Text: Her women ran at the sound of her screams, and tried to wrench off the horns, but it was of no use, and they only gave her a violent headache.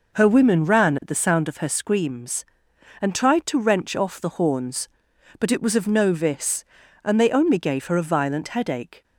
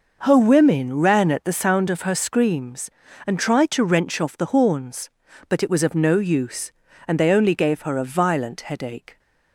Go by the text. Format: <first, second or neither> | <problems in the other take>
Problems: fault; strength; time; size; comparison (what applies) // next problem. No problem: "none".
second | says "vis" for "use"; at 6.1 s